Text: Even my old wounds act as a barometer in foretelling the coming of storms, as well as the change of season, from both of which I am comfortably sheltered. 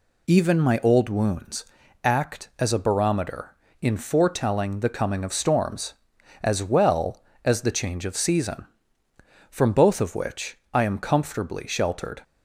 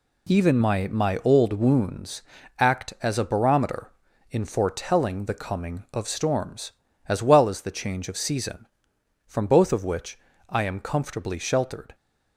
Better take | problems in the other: first | says "my" twice; at 0.8 s // pauses between "wounds" and "act"; slight; at 2.2 s; 0.36 s long; also in the first // pauses between "which" and "I"; slight; at 10.1 s; 0.32 s long

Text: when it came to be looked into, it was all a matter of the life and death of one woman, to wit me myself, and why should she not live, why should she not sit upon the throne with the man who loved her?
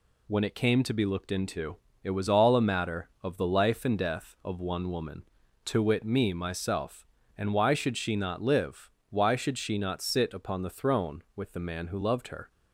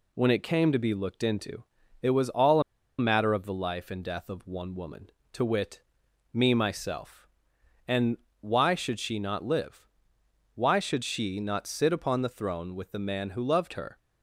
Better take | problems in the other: first | pauses between "a" and "matter"; at 2.6 s; 0.37 s long // pauses between "wit" and "me"; noticeable; at 5.7 s; 0.52 s long // pauses between "and" and "why"; slight; at 8.1 s; 0.24 s long

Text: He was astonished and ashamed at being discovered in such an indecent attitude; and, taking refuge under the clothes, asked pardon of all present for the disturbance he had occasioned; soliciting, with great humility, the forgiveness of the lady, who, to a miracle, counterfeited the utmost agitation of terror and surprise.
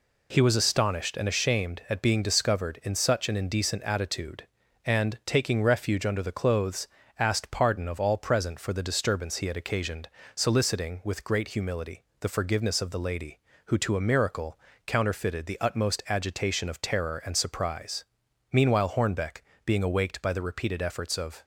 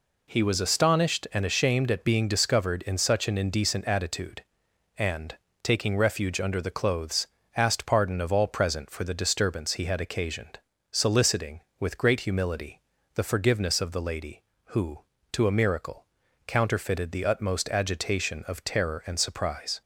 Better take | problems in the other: second | goes on to say "Meanwhile Hornbeck being awaked by the repeated efforts of"; strong; from 18.5 s on; 2.9 s long

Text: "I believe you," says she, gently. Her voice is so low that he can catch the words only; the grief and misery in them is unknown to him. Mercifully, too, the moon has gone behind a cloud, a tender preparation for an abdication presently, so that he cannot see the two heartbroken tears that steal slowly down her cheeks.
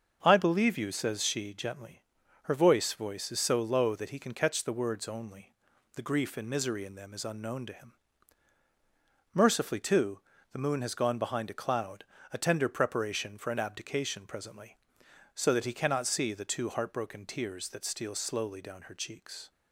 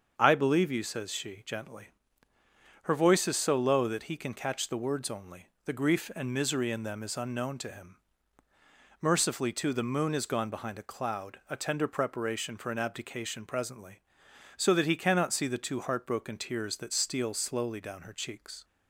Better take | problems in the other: second | starts louder than the rest; until 1.2 s; 6.5 dB; also in the second // says "voice" twice; at 2.9 s

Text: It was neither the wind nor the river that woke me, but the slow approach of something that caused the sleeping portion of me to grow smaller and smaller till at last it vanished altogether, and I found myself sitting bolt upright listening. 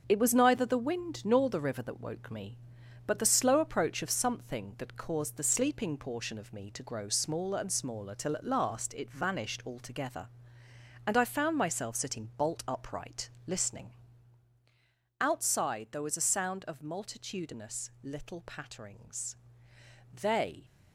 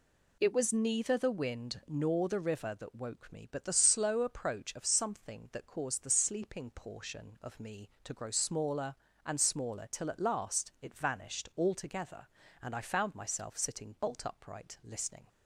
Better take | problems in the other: second | starts louder than the rest; until 1.0 s; 6.5 dB // pauses between "upright" and "listening"; slight; at 13.2 s; 0.18 s long // goes on to say "Outside there was a sound of multitudinous little patterings They"; strong; from 15.1 s on; 5.4 s long

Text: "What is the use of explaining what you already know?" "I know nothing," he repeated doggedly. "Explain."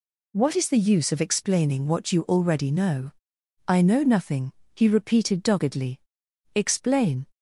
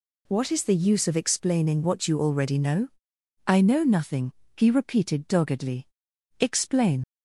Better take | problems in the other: first | leaves "Explain" unfinished; at 7.0 s; 65 ms

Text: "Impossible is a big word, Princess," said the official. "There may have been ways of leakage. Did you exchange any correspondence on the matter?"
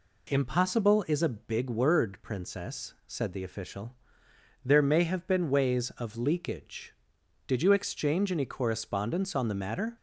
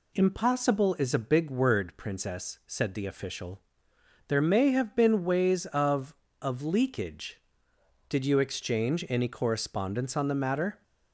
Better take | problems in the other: first | says "of" twice; at 6.3 s

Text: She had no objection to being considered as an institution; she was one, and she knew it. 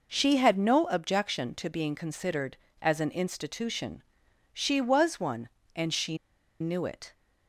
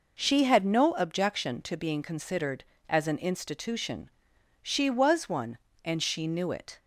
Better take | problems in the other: second | pauses between "she" and "knew"; at 6.1 s; 0.44 s long

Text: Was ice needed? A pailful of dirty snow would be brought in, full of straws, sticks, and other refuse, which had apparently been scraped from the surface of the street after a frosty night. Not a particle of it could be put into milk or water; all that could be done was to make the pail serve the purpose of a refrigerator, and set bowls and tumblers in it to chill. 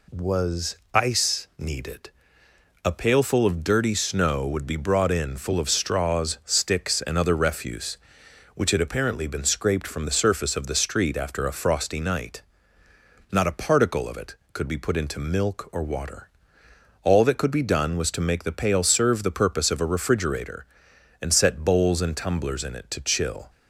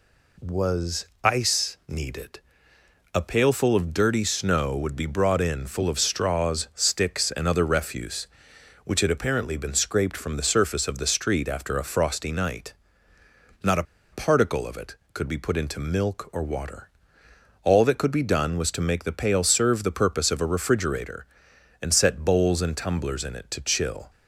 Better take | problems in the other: first | pauses between "Was" and "ice"; slight; at 1.0 s; 0.16 s long; slight in the first // pauses between "a" and "particle"; slight; at 13.8 s; 0.29 s long

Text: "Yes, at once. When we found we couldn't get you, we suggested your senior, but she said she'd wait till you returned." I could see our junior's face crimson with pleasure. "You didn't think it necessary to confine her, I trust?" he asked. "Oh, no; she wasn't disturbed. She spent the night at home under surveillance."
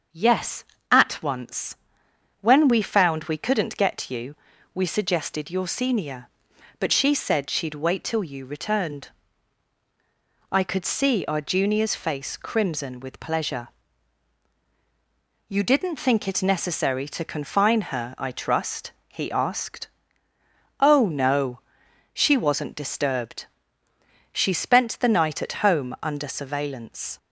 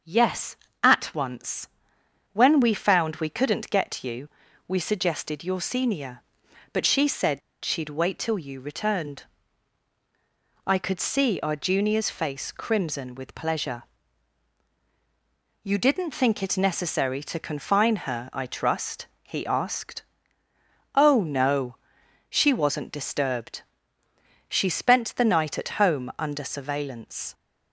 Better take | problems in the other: first | starts louder than the rest; until 1.2 s; 6.5 dB; also in the first // pauses between "said" and "she'd"; slight; at 7.4 s; 0.22 s long

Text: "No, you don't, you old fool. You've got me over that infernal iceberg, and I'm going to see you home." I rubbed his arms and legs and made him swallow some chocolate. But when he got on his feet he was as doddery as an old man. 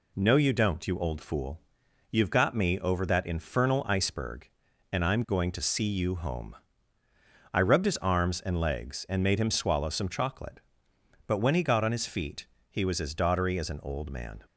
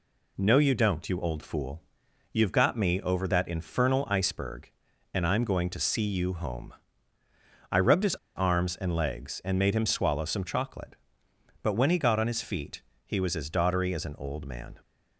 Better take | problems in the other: first | pauses between "his" and "arms"; slight; at 8.1 s; 0.19 s long // pauses between "feet" and "he"; slight; at 12.8 s; 0.20 s long; slight in the first

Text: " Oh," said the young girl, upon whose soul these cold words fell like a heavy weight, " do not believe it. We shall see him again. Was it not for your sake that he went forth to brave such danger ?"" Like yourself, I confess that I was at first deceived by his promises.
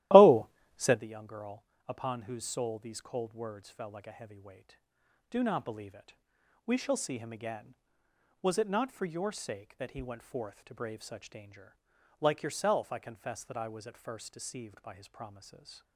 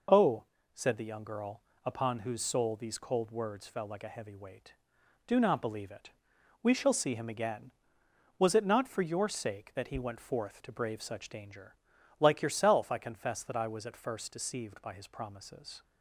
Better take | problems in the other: second | starts louder than the rest; strong; until 1.0 s; 15.5 dB

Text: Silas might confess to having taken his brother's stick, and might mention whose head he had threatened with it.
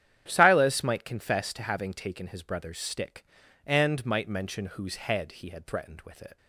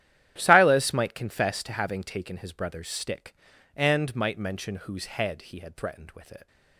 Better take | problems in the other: first | gets quieter; strong; throughout; 17 dB // starts louder than the rest; strong; until 1.3 s; 11 dB; strong in the first

